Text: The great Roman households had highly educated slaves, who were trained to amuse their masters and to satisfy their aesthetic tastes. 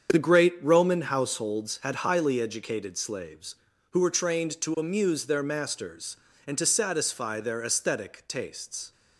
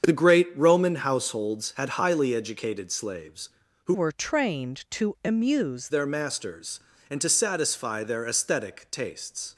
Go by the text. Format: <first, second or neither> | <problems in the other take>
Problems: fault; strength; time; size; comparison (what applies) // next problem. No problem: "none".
first | starts louder than the rest; strong; until 1.1 s; 8 dB; strong in the first // changes voice from "were" to "amuse"; from 3.9 to 5.8 s; 1.9 s long